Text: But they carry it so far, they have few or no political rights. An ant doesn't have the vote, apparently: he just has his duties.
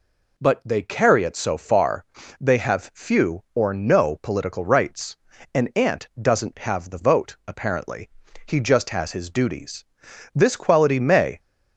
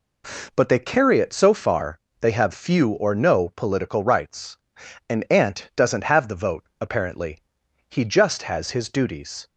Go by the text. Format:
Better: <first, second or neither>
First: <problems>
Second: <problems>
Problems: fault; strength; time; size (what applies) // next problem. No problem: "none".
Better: second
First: goes on to say "This quality may"; noticeable; from 10.3 s on; 1.0 s long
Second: none